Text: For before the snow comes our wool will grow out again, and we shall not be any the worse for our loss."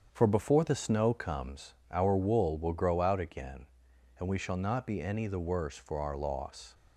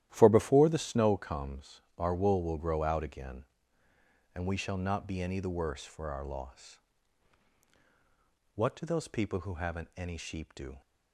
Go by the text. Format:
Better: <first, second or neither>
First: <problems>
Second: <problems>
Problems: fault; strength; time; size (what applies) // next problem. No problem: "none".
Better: first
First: starts louder than the rest; strong; until 1.1 s; 7.5 dB // pauses between "comes" and "our"; slight; at 1.7 s; 0.18 s long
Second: starts louder than the rest; strong; until 1.1 s; 12.5 dB // pauses between "comes" and "our"; slight; at 1.8 s; 0.16 s long // goes on to say "What do those people who haven't any sheep do"; strong; from 8.5 s on; 2.2 s long